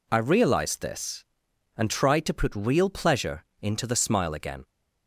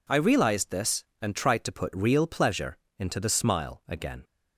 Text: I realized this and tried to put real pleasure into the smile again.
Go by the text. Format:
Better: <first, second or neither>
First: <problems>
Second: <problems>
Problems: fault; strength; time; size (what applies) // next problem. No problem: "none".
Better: neither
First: pauses between "pleasure" and "into"; slight; at 3.4 s; 0.16 s long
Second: pauses between "pleasure" and "into"; slight; at 2.7 s; 0.20 s long